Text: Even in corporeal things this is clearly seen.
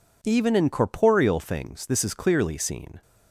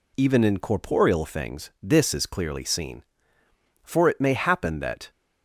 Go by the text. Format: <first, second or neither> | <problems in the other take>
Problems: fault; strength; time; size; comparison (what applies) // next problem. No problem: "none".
first | goes on to say "For it may happen that"; noticeable; from 3.8 s on; 1.2 s long